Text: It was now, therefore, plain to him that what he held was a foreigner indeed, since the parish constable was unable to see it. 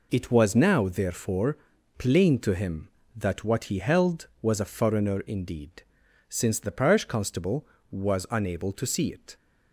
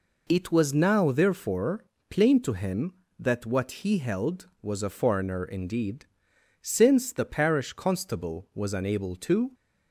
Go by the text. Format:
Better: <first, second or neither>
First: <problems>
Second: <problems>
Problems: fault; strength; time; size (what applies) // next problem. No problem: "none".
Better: first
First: none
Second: stops before "see it"; at 9.5 s